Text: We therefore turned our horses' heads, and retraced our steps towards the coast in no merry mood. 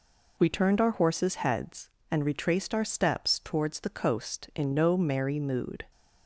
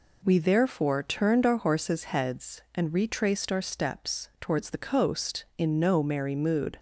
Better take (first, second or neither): second